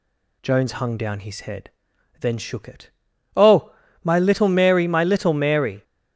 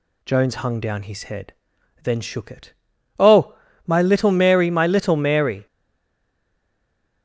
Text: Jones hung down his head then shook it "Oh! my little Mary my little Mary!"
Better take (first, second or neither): first